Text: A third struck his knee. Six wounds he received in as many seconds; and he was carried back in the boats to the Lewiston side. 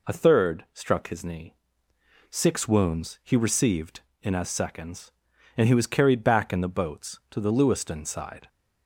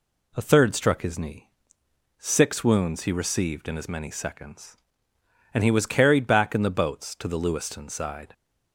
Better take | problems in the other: second | skips "many"; at 4.4 s

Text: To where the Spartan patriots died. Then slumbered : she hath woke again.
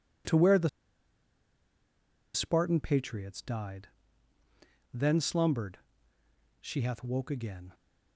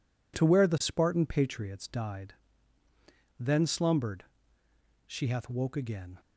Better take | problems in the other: second | pauses between "the" and "Spartan"; strong; at 0.6 s; 1.6 s long

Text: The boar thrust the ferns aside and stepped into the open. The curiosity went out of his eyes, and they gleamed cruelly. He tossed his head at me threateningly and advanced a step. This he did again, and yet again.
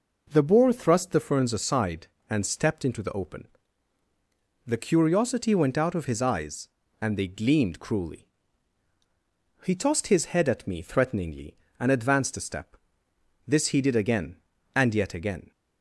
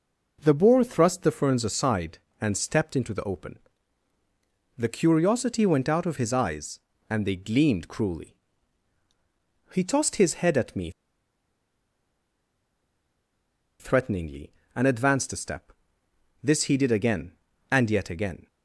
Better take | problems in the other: first | pauses between "me" and "threateningly"; strong; at 10.9 s; 2.8 s long

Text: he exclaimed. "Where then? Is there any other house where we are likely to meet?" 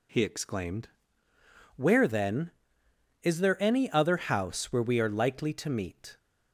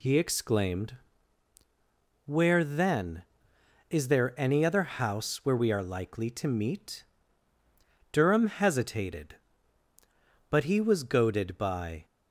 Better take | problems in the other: first | goes on to say "Durham hesitated but he was goaded by"; strong; from 8.1 s on; 3.9 s long

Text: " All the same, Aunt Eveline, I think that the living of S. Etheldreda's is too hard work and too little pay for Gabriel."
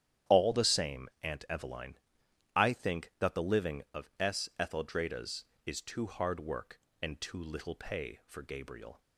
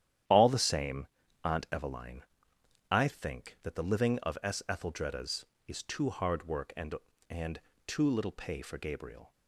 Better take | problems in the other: first | starts louder than the rest; strong; until 1.6 s; 11 dB; strong in the first // says "and" twice; at 7.2 s

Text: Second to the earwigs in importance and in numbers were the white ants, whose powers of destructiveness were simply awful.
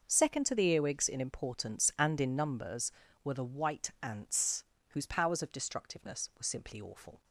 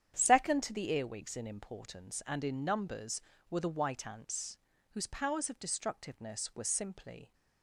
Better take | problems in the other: first | starts louder than the rest; strong; until 1.1 s; 9 dB // stops before "awful"; at 7.3 s

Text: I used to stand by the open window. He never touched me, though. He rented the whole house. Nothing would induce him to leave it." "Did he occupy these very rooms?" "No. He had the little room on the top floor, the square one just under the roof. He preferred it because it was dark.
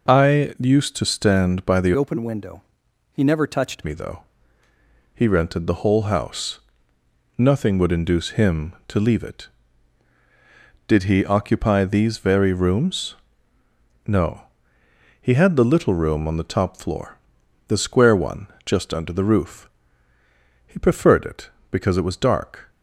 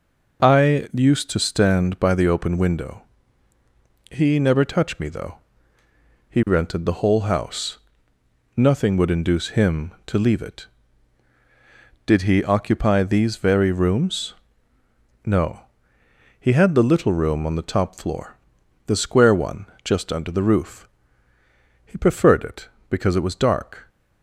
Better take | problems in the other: second | changes voice from "open" to "touched"; from 1.9 to 3.8 s; 1.9 s long // pauses between "one" and "just"; slight; at 18.4 s; 0.18 s long; slight in the second

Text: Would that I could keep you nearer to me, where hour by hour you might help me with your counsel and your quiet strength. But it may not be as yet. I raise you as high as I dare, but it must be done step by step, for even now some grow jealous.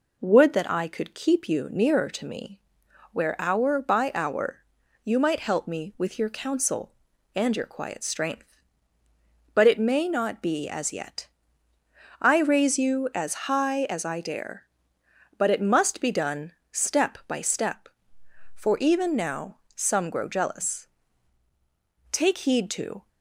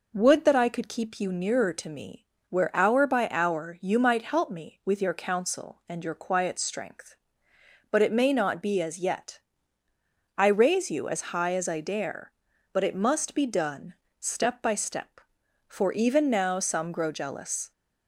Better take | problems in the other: second | pauses between "hour" and "you"; at 4.6 s; 0.40 s long // pauses between "done" and "step"; slight; at 16.5 s; 0.20 s long; slight in the second // pauses between "now" and "some"; slight; at 19.5 s; 0.18 s long // goes on to say "Take heed to"; noticeable; from 22.0 s on; 0.98 s long

